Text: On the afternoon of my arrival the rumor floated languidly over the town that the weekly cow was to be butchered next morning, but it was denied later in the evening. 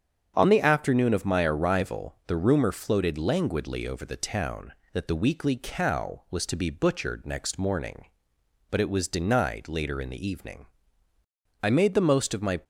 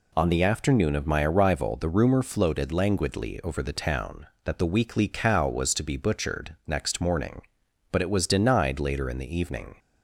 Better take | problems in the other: second | starts louder than the rest; strong; until 1.3 s; 7.5 dB // goes on to say "I made the most of my"; noticeable; from 11.6 s on; 0.98 s long

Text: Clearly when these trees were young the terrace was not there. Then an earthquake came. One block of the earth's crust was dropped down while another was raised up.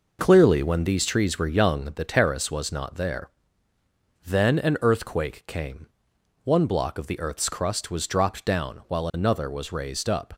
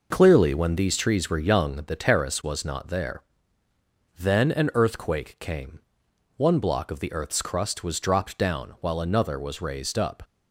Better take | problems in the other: neither | none

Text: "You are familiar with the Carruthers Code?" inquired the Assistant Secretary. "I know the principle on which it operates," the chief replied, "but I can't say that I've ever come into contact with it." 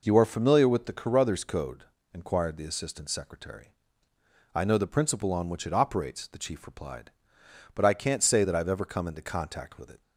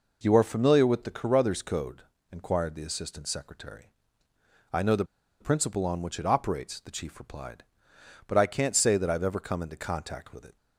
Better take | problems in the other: first | pauses between "the" and "principle"; at 5.0 s; 0.36 s long

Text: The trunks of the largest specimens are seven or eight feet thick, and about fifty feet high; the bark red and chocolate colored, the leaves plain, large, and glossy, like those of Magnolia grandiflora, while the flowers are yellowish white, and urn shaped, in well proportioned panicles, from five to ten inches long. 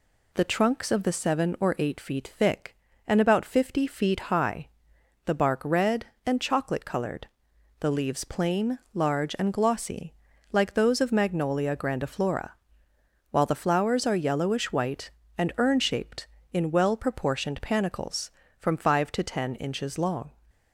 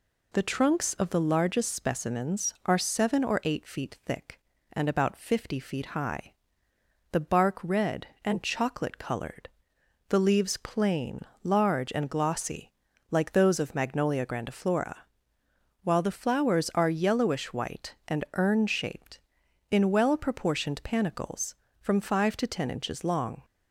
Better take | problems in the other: second | skips "largest specimens are"; at 1.1 s

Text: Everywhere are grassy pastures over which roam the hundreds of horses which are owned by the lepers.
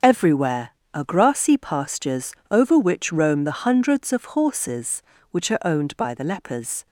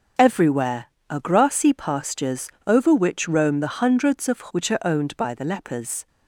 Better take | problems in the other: first | starts louder than the rest; until 1.4 s; 6.5 dB; also in the first // pauses between "pastures" and "over"; slight; at 2.4 s; 0.18 s long; slight in the first // skips "horses"; at 4.4 s

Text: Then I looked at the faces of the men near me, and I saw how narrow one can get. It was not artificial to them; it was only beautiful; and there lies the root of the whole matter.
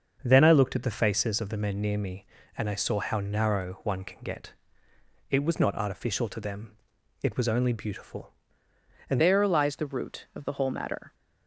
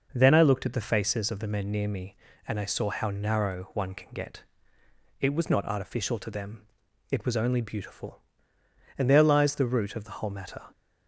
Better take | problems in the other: second | starts louder than the rest; until 1.2 s; 6.5 dB // changes voice at "there"; from 9.1 s on; 2.0 s long

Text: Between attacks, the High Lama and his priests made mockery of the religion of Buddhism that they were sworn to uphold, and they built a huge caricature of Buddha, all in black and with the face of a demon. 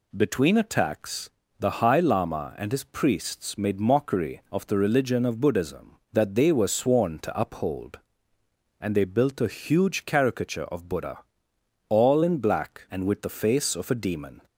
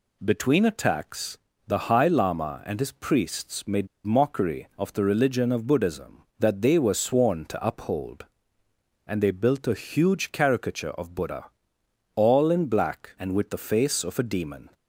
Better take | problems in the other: first | pauses between "made" and "mockery"; slight; at 3.8 s; 0.19 s long

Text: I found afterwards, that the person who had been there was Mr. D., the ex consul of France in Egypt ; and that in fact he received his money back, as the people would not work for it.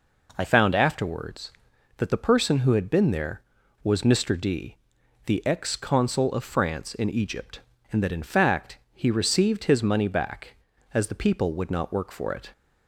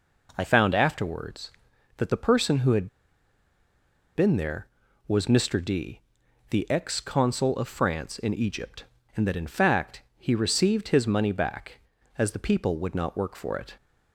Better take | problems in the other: first | pauses between "had" and "been"; strong; at 2.8 s; 1.2 s long // pauses between "fact" and "he"; slight; at 10.0 s; 0.16 s long; slight in the first

